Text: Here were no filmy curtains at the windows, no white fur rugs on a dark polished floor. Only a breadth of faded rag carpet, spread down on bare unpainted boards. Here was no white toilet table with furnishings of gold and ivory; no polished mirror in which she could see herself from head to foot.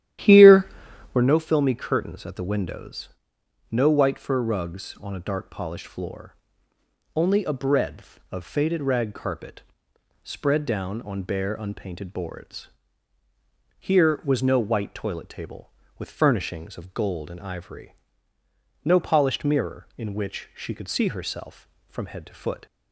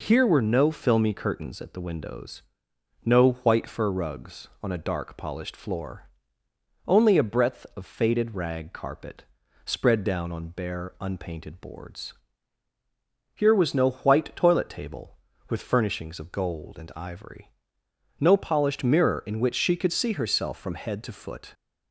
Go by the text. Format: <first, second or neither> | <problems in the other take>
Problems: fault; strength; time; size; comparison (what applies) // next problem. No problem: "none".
second | starts louder than the rest; strong; until 1.3 s; 12 dB